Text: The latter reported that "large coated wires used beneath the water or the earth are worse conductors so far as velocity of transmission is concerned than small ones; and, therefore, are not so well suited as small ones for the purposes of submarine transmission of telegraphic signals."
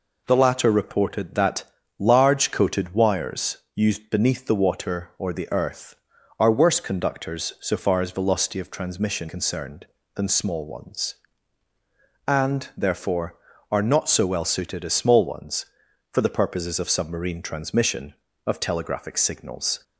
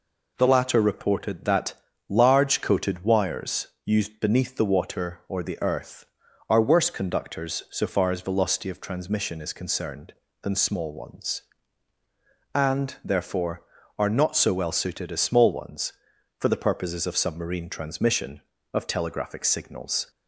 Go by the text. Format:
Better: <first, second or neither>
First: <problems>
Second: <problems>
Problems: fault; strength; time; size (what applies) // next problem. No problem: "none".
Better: second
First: pauses between "that" and "large"; slight; at 1.6 s; 0.34 s long // pauses between "wires" and "used"; slight; at 3.5 s; 0.16 s long // skips "is"; at 9.2 s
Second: pauses between "that" and "large"; slight; at 1.7 s; 0.34 s long // pauses between "wires" and "used"; slight; at 3.6 s; 0.16 s long